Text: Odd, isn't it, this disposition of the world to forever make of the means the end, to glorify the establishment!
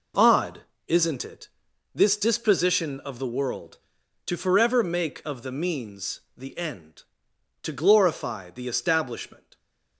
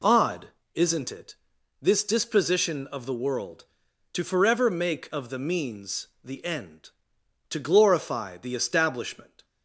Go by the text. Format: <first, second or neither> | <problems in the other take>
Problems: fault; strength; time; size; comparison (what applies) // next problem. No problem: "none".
second | gets quieter; strong; throughout; 9 dB // pauses between "means" and "the"; slight; at 6.2 s; 0.16 s long; slight in the second